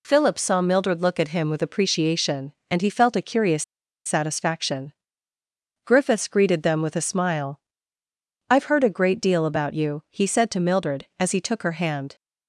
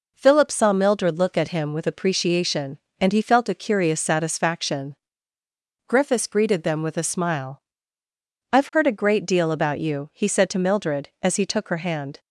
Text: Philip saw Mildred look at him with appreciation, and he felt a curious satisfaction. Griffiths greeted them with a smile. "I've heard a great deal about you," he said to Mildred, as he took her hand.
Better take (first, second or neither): second